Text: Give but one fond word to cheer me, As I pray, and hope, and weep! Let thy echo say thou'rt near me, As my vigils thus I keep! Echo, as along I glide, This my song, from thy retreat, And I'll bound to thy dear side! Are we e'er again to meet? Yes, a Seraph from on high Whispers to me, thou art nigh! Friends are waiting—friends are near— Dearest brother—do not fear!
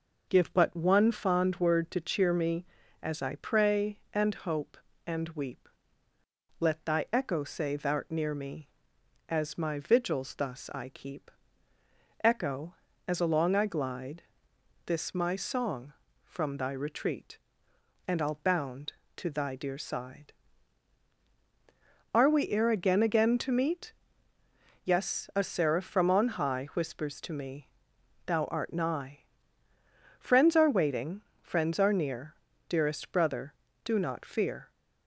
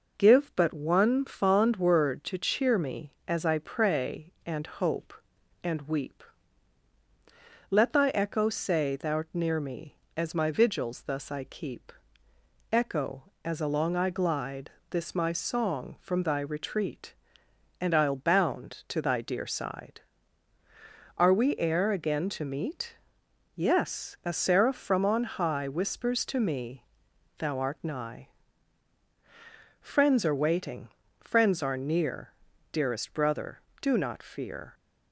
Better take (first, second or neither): second